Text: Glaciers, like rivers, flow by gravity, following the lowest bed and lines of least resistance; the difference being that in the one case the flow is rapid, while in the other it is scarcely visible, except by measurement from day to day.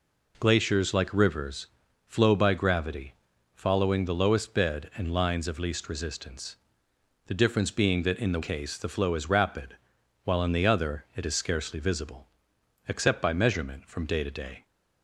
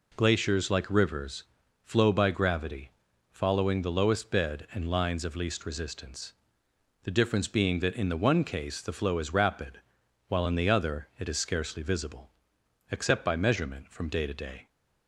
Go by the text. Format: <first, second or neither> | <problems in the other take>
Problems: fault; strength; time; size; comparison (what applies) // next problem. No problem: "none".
second | skips "one"; at 8.4 s